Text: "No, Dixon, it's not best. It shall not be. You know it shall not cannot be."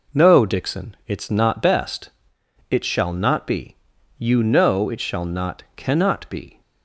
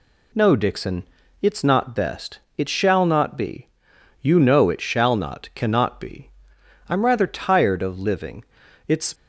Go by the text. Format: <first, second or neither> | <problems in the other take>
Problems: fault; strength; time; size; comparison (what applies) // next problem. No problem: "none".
first | goes on to say "I'm rather tired of living It's"; strong; from 6.8 s on; 2.2 s long